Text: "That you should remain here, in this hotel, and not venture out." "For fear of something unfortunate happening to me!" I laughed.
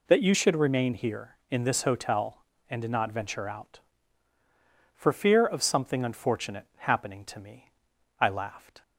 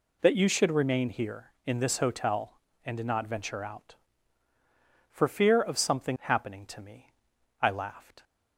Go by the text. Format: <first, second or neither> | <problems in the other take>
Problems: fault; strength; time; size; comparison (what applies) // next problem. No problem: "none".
first | skips "unfortunate"; at 6.1 s